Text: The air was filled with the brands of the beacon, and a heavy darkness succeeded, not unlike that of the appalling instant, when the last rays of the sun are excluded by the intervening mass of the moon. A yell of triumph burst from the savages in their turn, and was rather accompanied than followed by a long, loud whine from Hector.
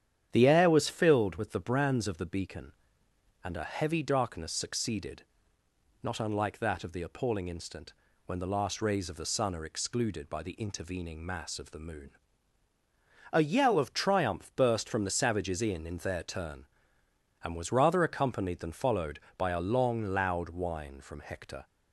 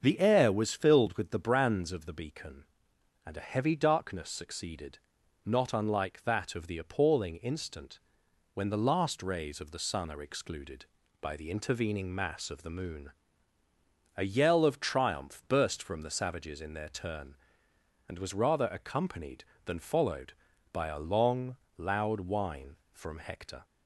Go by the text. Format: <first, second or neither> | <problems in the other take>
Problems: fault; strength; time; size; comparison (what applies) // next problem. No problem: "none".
second | starts louder than the rest; strong; until 1.3 s; 9.5 dB; also in the second // says "in" twice; at 15.8 s